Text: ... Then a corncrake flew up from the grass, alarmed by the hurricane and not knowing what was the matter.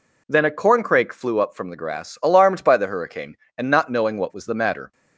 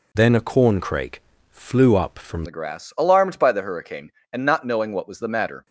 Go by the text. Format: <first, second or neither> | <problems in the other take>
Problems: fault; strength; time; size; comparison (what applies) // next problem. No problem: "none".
first | changes voice from "Then" to "from"; from 0.1 to 2.4 s; 2.3 s long // pauses between "corncrake" and "flew"; slight; at 1.2 s; 0.32 s long